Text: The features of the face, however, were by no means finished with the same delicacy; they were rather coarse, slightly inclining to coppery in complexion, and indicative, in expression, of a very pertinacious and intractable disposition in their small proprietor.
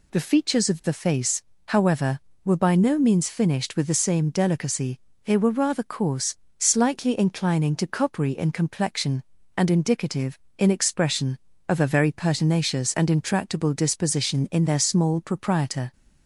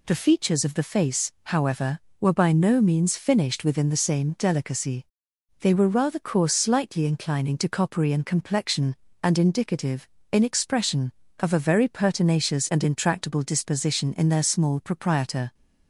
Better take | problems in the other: first | says "within" for "with"; at 3.6 s

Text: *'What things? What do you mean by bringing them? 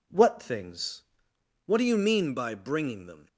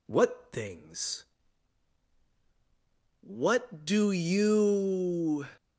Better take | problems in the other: first | stops before "mean by bringing them"; at 5.5 s

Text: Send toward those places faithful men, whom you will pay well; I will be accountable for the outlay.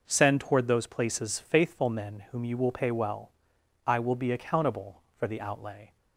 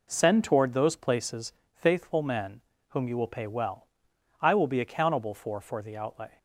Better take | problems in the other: first | pauses between "places" and "faithful"; slight; at 1.5 s; 0.22 s long // says "for" twice; at 5.5 s

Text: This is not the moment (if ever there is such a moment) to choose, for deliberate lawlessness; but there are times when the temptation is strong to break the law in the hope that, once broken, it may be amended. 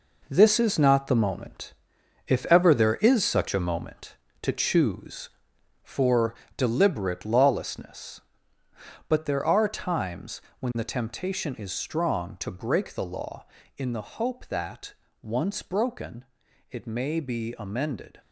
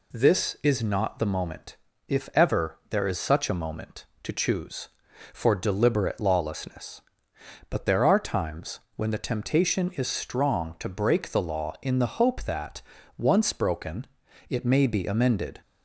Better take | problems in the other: second | gets quieter; strong; throughout; 9 dB // pauses between "for" and "deliberate"; slight; at 6.3 s; 0.22 s long // pauses between "times" and "when"; slight; at 10.3 s; 0.20 s long; slight in the second

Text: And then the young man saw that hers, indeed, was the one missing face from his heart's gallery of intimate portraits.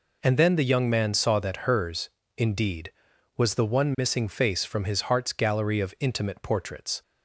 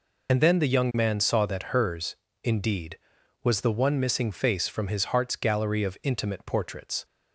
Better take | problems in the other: first | loses the start of "And"; at 0.2 s; 40 ms

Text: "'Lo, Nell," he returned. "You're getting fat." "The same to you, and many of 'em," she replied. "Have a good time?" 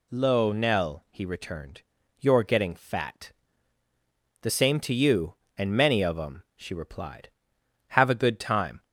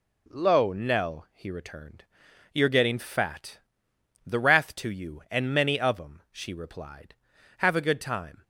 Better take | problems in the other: first | says "wrath" for "same"; at 4.3 s

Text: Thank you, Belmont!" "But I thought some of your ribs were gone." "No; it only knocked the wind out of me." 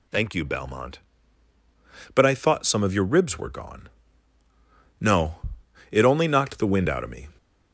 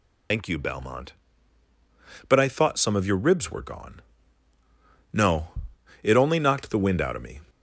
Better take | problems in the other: first | loses the start of "Thank"; at 0.3 s; 80 ms

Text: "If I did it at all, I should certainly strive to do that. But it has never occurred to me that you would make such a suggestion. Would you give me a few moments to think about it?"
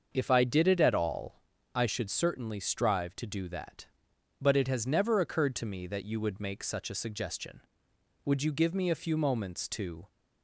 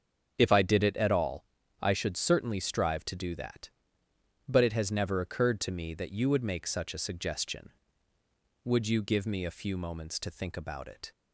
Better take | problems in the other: second | starts louder than the rest; until 1.1 s; 6.5 dB; also in the second // stops before "think about it"; at 10.0 s

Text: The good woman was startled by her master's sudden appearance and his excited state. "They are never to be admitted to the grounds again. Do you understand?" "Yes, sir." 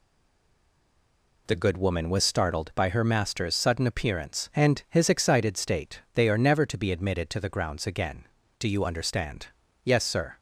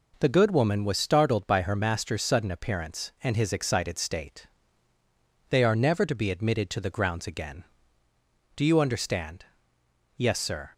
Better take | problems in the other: second | stays silent before the first word; noticeable; until 1.4 s; 1.4 s long

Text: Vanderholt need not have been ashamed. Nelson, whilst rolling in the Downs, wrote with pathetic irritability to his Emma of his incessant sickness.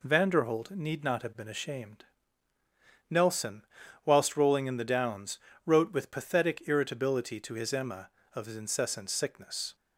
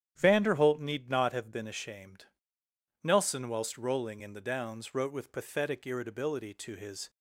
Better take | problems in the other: first | starts louder than the rest; strong; until 1.1 s; 10.5 dB // stops before "Emma of his incessant sickness"; at 7.0 s

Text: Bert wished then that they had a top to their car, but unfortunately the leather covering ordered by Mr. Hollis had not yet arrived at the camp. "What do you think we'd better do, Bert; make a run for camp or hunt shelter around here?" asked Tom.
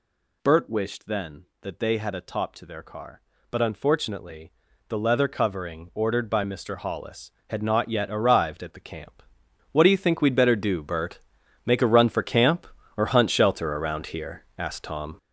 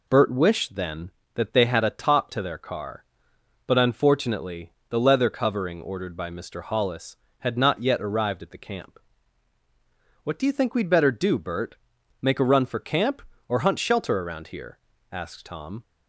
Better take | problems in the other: second | gets louder; strong; throughout; 8.5 dB // pauses between "unfortunately" and "the"; slight; at 4.5 s; 0.36 s long; slight in the second

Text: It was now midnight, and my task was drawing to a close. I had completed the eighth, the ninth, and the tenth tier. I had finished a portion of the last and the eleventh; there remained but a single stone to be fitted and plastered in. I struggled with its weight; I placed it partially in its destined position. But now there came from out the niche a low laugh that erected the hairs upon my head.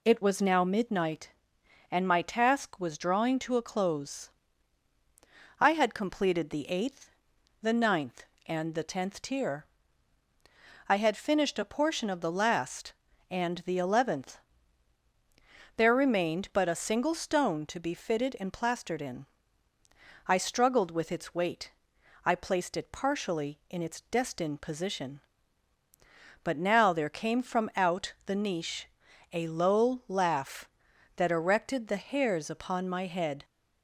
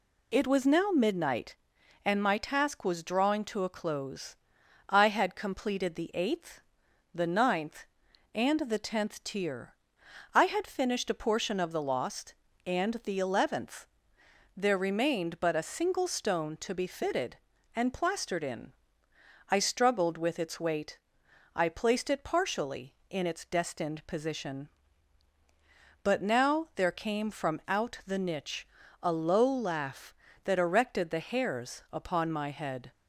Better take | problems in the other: first | says "lost" for "last"; at 11.8 s // pauses between "niche" and "a"; slight; at 28.6 s; 0.36 s long; noticeable in the first

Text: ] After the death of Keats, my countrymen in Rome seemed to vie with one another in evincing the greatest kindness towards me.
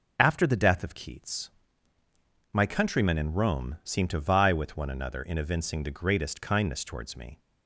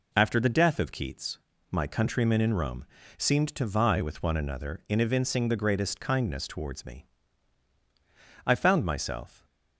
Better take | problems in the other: first | pauses between "Rome" and "seemed"; slight; at 2.8 s; 0.32 s long // goes on to say "I found myself"; noticeable; from 8.4 s on; 1.0 s long

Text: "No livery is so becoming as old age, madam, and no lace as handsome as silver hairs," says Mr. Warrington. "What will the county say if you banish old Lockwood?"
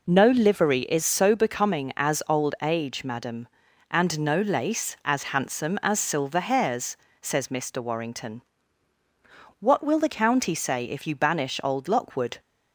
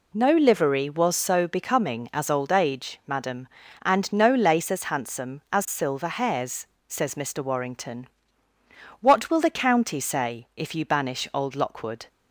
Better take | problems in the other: first | says "was" for "is"; at 0.8 s

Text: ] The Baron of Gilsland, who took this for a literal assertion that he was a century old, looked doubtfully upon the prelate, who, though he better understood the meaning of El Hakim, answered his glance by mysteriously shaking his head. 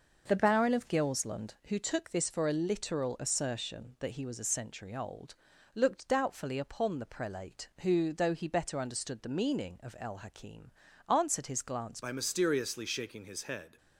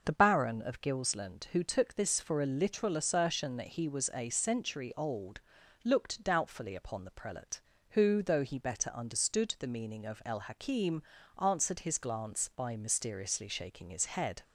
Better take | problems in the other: second | changes voice at "by"; from 12.0 s on; 1.7 s long

